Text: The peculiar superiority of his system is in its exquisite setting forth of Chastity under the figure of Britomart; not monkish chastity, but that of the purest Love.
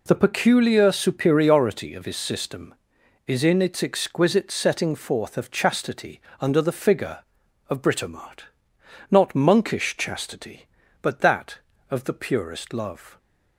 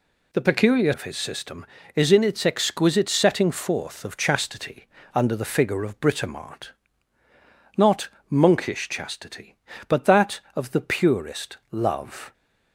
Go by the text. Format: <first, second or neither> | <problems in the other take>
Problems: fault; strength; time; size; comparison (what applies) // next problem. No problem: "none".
first | skips "superiority"; at 0.9 s // pauses between "Chastity" and "under"; slight; at 4.8 s; 0.28 s long; slight in the first // pauses between "not" and "monkish"; slight; at 8.0 s; 0.20 s long